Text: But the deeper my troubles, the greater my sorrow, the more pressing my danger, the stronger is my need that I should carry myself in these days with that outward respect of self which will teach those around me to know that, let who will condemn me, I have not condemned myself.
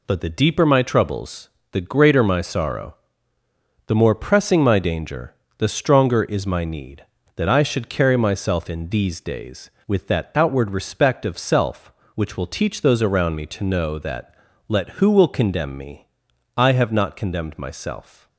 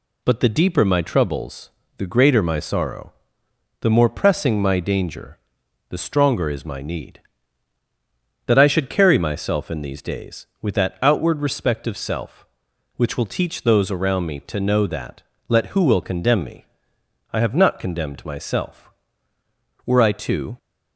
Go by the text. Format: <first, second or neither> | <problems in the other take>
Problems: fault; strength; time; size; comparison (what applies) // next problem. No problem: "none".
first | goes on to say "Were I to"; noticeable; from 19.8 s on; 0.72 s long